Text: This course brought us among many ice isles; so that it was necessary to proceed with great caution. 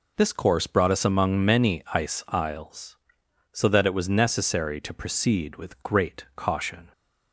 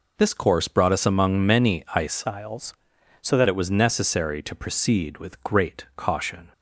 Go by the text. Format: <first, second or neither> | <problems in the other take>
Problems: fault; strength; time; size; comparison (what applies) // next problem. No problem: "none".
first | changes voice from "isles" to "that"; from 2.2 to 3.4 s; 1.2 s long